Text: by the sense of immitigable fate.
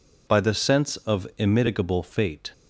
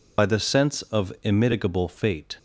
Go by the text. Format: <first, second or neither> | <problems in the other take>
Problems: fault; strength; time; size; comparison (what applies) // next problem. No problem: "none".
first | loses the start of "by"; at 0.1 s; 45 ms